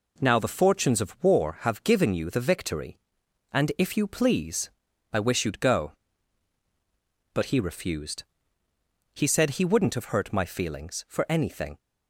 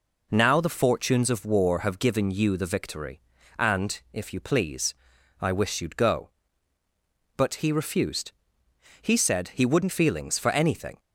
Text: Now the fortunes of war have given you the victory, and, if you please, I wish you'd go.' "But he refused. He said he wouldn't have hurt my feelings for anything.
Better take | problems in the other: first | skips "have hurt my"; at 9.8 s

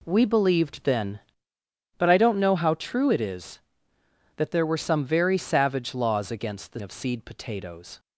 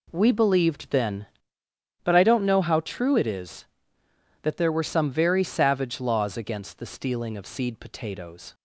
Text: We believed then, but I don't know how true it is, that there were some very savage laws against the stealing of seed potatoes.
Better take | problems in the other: second | skips "stealing"; at 6.8 s

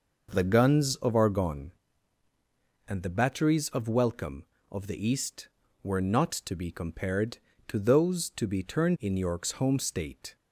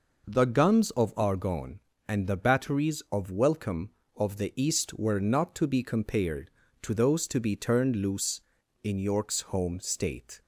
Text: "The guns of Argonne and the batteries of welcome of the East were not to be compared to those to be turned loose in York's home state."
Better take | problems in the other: second | skips "loose"; at 8.9 s

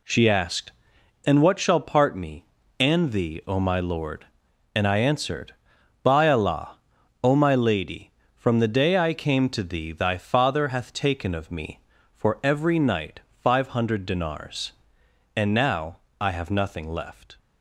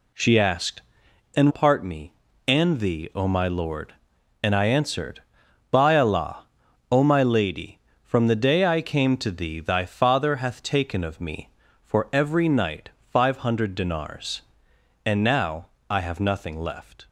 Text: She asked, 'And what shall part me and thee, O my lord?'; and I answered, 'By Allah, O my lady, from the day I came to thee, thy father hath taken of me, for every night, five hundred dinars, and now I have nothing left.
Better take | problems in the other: first | skips "what shall"; at 1.5 s // pauses between "now" and "I"; slight; at 15.6 s; 0.22 s long; slight in the first

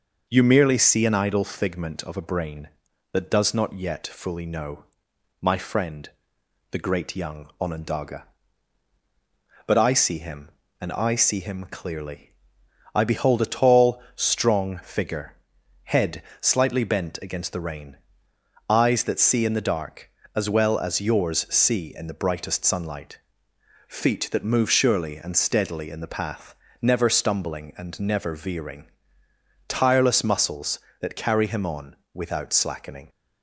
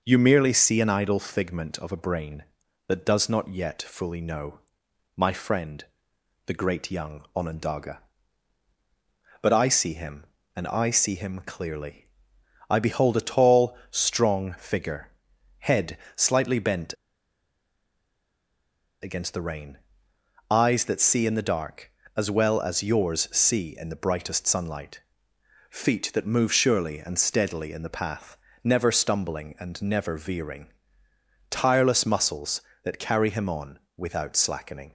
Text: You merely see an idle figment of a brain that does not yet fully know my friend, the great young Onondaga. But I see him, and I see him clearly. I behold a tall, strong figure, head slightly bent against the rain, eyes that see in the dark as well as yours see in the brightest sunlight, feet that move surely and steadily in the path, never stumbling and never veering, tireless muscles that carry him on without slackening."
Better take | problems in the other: first | pauses between "know" and "my"; noticeable; at 4.5 s; 0.56 s long; noticeable in the first // pauses between "head" and "slightly"; slight; at 15.9 s; 0.20 s long; slight in the first // pauses between "bent" and "against"; strong; at 16.9 s; 2.0 s long // pauses between "on" and "without"; slight; at 33.7 s; 0.18 s long; slight in the first

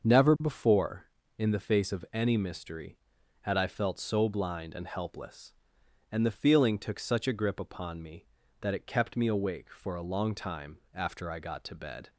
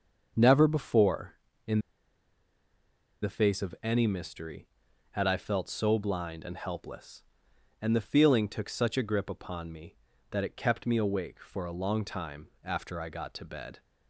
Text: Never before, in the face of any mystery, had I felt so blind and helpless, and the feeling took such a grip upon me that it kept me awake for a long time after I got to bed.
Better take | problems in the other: first | starts louder than the rest; until 1.6 s; 6.5 dB; also in the first // pauses between "in" and "the"; strong; at 1.7 s; 1.4 s long // pauses between "time" and "after"; slight; at 12.4 s; 0.16 s long; slight in the first

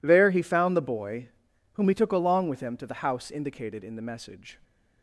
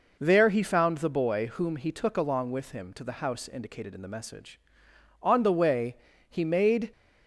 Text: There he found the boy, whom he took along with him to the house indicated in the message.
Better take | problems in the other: first | goes on to say "On the way he made"; strong; from 5.2 s on; 1.7 s long

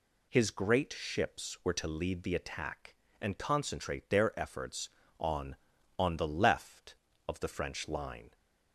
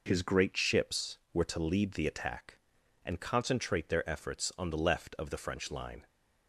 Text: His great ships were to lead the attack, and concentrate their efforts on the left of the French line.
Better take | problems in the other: second | says "on" twice; at 5.9 s

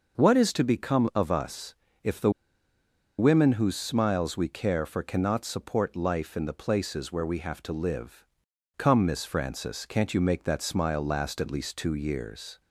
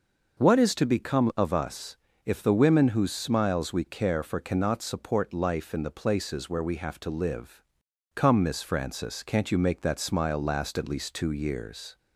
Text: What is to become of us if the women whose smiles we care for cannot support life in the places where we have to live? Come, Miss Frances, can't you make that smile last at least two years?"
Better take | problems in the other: second | pauses between "us" and "if"; slight; at 1.7 s; 0.28 s long; slight in the second // pauses between "the" and "women"; noticeable; at 2.3 s; 0.86 s long

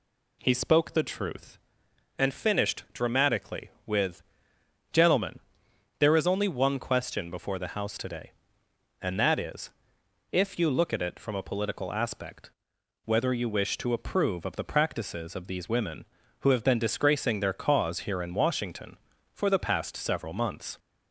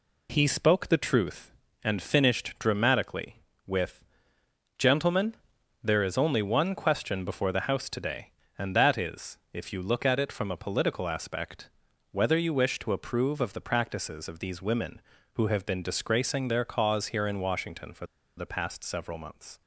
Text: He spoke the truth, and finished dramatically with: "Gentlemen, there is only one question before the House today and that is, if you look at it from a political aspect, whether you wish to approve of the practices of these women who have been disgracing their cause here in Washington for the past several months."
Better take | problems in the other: first | pauses between "for" and "the"; slight; at 18.0 s; 0.30 s long

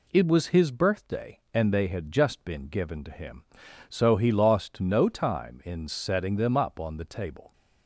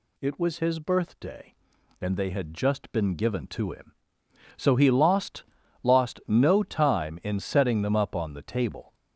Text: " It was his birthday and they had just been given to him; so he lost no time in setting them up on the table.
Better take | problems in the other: first | says "lost" twice; at 5.8 s

